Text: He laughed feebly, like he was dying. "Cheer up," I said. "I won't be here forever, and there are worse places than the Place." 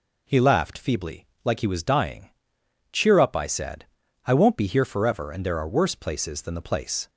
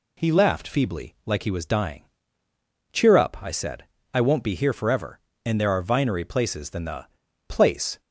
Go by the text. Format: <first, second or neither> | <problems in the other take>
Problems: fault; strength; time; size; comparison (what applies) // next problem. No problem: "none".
first | says "vinery" for "worse"; at 5.8 s // pauses between "the" and "Place"; at 7.0 s; 0.42 s long